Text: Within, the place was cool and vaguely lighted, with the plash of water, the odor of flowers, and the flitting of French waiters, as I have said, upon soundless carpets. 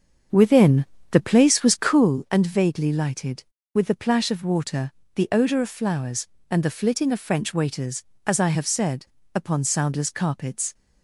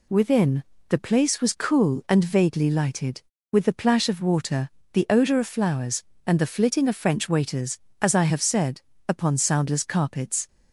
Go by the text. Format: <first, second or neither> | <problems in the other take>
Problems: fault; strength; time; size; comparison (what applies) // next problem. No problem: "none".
second | starts louder than the rest; until 2.2 s; 7 dB